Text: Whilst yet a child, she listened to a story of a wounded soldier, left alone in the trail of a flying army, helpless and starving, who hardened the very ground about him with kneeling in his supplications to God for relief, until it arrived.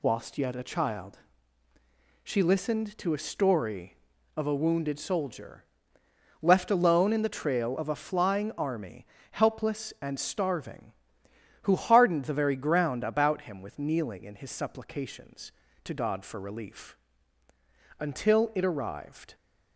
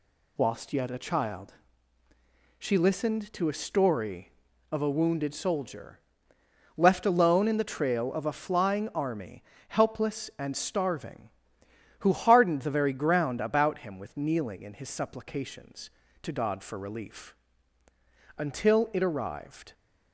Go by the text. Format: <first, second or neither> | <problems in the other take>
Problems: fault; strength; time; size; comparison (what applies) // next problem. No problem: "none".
neither | none